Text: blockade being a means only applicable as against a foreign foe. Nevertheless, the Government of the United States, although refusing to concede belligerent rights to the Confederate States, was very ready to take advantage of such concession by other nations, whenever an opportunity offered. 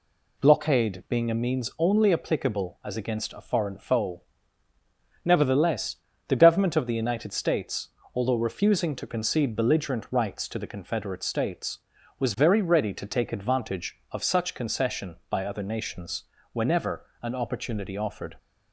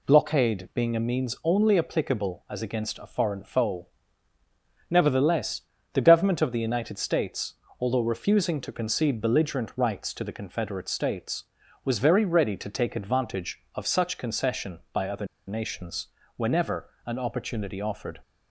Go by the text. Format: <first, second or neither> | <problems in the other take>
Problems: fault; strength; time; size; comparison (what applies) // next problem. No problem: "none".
first | pauses between "other" and "nations"; slight; at 15.2 s; 0.22 s long // pauses between "whenever" and "an"; slight; at 16.8 s; 0.16 s long; slight in the first